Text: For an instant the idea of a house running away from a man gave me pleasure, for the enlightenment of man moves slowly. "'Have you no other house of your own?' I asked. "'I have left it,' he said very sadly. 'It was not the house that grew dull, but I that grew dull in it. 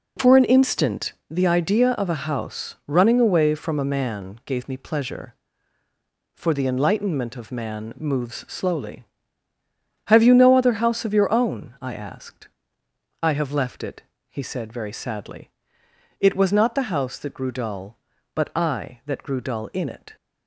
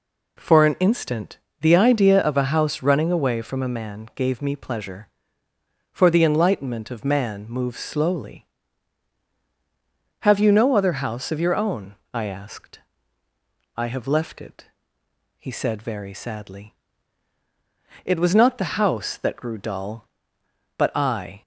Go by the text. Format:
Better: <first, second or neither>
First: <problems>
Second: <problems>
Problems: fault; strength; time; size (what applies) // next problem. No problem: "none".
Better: first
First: pauses between "instant" and "the"; slight; at 1.1 s; 0.16 s long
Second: pauses between "instant" and "the"; slight; at 1.3 s; 0.22 s long // stops before "that grew dull in it"; at 21.4 s